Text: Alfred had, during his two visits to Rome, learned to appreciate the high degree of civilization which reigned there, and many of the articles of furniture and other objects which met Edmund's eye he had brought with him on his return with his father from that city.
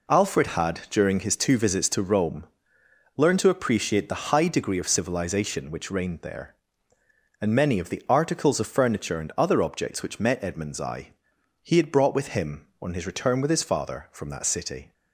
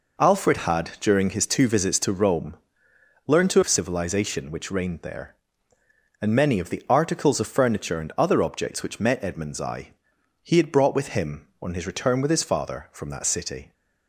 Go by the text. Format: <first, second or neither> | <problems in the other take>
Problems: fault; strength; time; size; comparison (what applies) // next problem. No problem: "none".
first | skips "appreciate the high degree"; at 3.6 s // pauses between "eye" and "he"; noticeable; at 9.9 s; 0.54 s long; noticeable in the first